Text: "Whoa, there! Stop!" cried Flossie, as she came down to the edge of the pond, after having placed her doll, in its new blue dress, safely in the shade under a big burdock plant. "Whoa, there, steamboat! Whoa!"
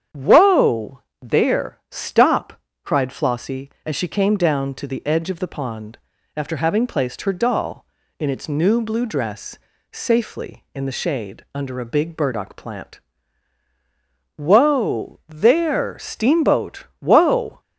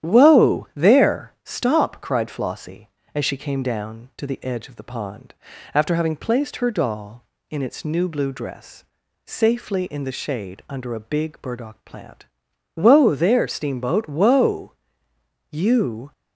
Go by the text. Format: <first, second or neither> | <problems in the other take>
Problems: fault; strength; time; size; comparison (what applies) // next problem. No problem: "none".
first | starts louder than the rest; strong; until 1.1 s; 10.5 dB; strong in the first // goes on to say "You"; noticeable; from 15.4 s on; 0.62 s long